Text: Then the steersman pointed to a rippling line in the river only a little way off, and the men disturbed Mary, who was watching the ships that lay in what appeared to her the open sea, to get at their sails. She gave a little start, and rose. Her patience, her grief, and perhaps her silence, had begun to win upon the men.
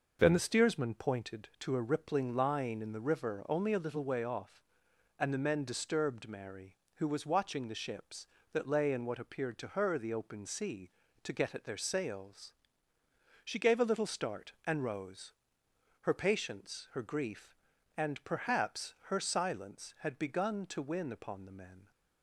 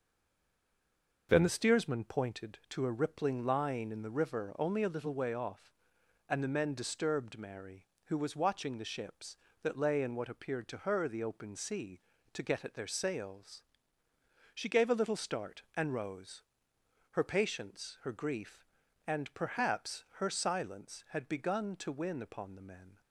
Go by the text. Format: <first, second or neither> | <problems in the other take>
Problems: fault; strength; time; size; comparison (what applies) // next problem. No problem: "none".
first | stays silent before the first word; noticeable; until 1.2 s; 1.2 s long // starts louder than the rest; noticeable; until 2.3 s; 6 dB